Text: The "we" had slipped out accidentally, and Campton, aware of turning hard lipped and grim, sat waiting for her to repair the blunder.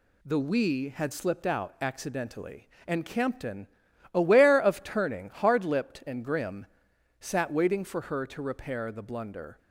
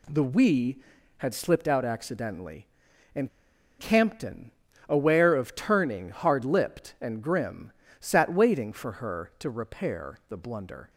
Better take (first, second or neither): first